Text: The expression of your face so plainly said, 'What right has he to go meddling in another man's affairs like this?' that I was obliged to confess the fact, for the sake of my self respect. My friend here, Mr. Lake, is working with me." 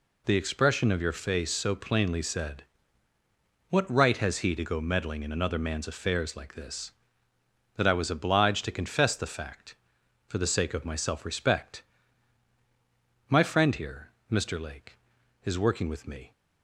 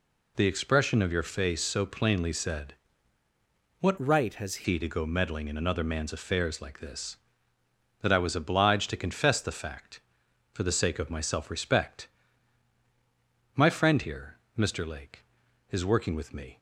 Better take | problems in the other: first | changes voice from "right" to "has"; from 3.9 to 4.6 s; 0.7 s long

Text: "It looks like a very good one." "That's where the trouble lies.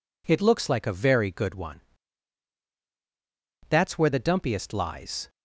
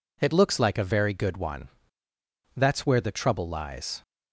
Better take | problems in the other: second | says "dumpiest" for "trouble"; at 4.1 s

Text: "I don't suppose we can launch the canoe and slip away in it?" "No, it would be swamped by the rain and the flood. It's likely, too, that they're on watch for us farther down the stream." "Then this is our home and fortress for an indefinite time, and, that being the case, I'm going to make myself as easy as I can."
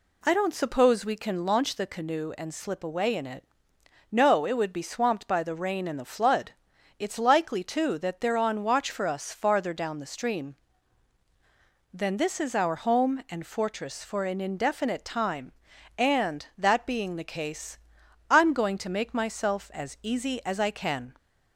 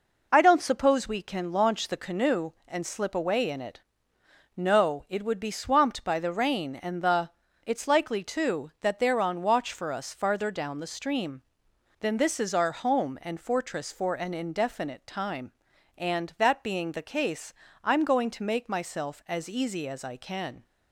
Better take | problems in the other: first | skips "flood"; at 7.4 s

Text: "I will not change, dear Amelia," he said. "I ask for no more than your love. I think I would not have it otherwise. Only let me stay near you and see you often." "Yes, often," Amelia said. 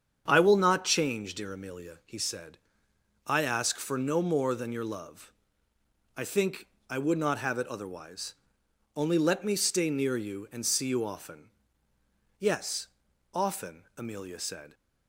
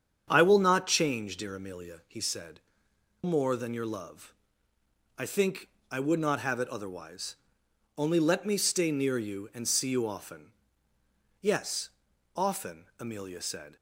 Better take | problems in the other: first | starts louder than the rest; strong; until 1.3 s; 8 dB; strong in the first // skips "I ask for no"; at 2.9 s // pauses between "think" and "I"; slight; at 5.6 s; 0.22 s long; slight in the first

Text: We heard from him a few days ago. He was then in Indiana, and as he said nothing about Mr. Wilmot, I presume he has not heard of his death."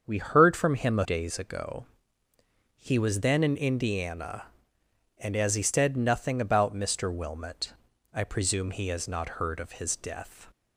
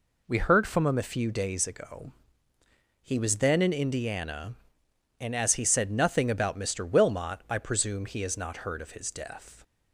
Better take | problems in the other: second | starts louder than the rest; until 1.0 s; 7 dB // skips "few"; at 1.0 s

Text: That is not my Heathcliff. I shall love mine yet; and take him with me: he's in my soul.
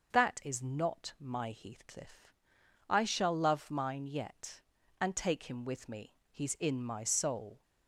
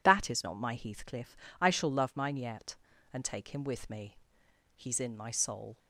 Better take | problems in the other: neither | none

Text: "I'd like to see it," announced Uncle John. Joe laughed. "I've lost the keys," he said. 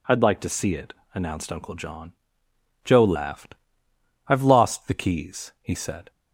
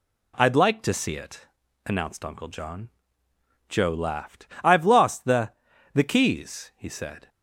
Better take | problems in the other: first | says "the" twice; at 5.9 s

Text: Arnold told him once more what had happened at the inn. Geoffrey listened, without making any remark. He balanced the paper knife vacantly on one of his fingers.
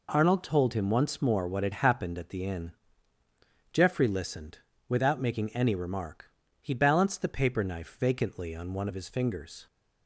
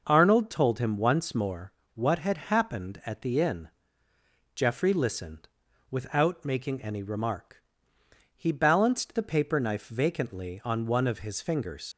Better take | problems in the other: first | pauses between "more" and "what"; slight; at 1.7 s; 0.23 s long // leaves "fingers" unfinished; at 11.9 s; 95 ms

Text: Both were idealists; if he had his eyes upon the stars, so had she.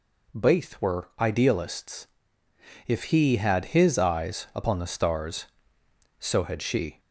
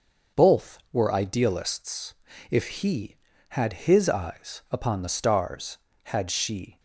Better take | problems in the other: first | starts louder than the rest; noticeable; until 1.4 s; 6 dB // skips "so"; at 5.9 s

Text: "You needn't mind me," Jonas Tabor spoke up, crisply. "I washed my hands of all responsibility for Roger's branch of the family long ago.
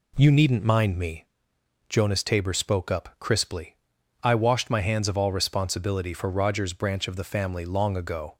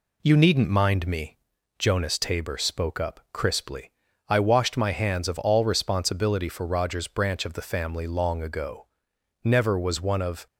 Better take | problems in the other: first | goes on to say "Never was one of"; noticeable; from 9.4 s on; 1.0 s long

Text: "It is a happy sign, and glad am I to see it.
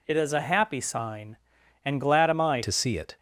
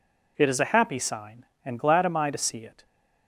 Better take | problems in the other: second | changes voice at "to"; from 2.6 s on; 0.5 s long

